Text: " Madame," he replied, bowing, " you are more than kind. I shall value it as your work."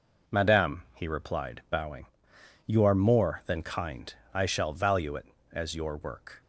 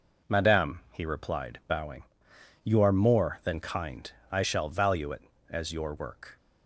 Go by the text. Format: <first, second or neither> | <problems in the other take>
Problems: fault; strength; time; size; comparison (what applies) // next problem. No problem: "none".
neither | none